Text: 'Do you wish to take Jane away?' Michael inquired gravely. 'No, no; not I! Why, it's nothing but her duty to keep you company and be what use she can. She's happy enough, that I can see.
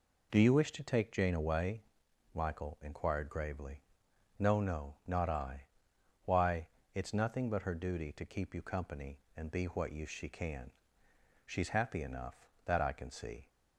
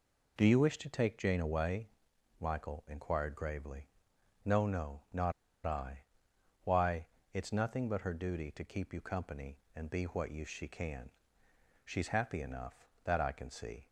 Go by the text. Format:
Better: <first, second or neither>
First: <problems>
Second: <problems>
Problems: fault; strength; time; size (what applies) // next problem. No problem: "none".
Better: first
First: none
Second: pauses between "not" and "I"; slight; at 5.3 s; 0.33 s long